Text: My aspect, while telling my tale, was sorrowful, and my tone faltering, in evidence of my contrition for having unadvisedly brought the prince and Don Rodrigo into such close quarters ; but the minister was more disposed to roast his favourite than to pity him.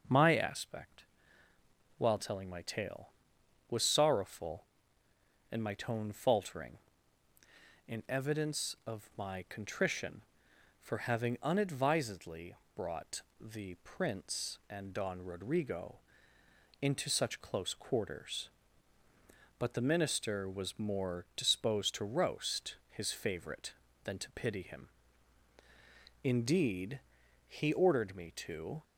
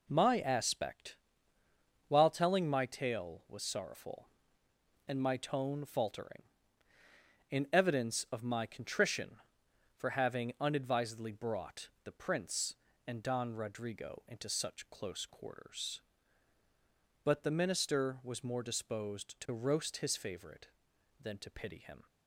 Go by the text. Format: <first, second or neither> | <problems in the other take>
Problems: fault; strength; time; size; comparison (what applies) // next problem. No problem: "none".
second | pauses between "unadvisedly" and "brought"; slight; at 12.5 s; 0.19 s long // pauses between "brought" and "the"; slight; at 13.2 s; 0.20 s long // pauses between "Rodrigo" and "into"; noticeable; at 15.9 s; 0.82 s long // goes on to say "Indeed he ordered me to"; strong; from 26.2 s on; 2.6 s long